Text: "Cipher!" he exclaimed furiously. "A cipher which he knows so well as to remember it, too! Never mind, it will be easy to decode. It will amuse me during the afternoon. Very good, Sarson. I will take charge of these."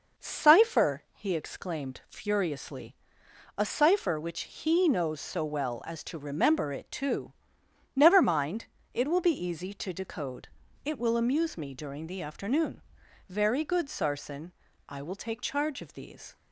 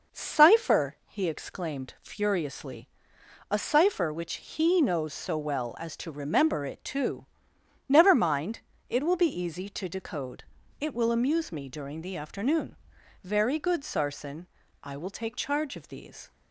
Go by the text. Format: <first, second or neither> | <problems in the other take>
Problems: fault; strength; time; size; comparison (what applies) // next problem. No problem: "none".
neither | none